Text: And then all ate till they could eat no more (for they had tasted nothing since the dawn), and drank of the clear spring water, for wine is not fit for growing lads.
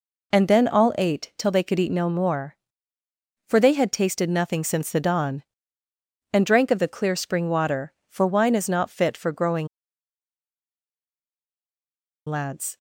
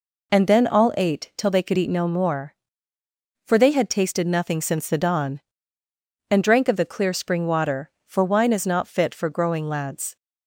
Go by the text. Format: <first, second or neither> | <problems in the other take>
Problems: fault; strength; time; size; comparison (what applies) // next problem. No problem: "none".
second | pauses between "growing" and "lads"; strong; at 9.6 s; 2.6 s long